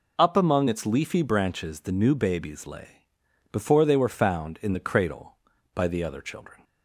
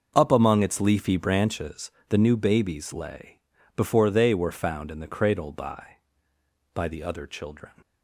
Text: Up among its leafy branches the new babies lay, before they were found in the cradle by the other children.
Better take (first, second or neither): first